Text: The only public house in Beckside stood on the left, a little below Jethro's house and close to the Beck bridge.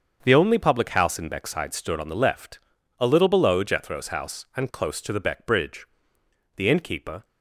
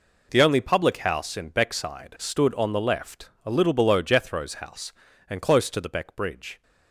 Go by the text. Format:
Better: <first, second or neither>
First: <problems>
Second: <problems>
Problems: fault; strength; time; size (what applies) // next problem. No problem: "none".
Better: second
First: starts louder than the rest; until 1.2 s; 7 dB // goes on to say "The innkeeper"; noticeable; from 6.5 s on; 0.68 s long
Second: none